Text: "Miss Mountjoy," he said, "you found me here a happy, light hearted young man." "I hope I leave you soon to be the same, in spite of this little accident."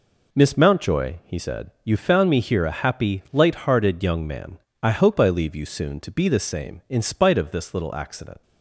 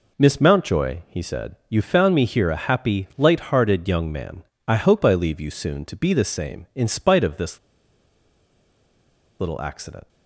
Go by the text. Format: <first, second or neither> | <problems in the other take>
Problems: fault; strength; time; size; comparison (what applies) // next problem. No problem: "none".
first | pauses between "this" and "little"; strong; at 7.5 s; 1.8 s long